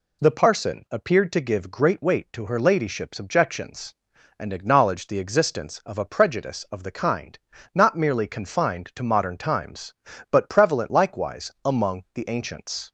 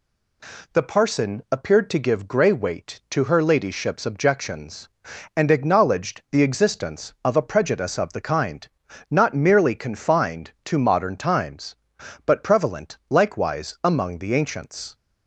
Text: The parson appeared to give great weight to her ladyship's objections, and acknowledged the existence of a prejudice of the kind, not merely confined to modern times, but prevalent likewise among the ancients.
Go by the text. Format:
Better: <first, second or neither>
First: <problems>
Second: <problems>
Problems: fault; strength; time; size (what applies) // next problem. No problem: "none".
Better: first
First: none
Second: says "grey" for "great"; at 2.2 s